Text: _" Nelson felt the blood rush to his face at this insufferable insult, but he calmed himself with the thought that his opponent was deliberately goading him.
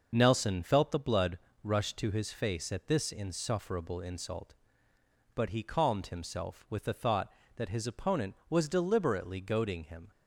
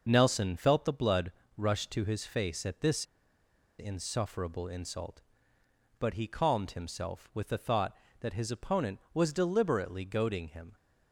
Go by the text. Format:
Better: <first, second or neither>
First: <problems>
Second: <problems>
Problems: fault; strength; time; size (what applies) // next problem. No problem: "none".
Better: first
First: pauses between "blood" and "rush"; slight; at 1.3 s; 0.24 s long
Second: pauses between "blood" and "rush"; slight; at 1.3 s; 0.24 s long // pauses between "this" and "insufferable"; noticeable; at 3.0 s; 0.75 s long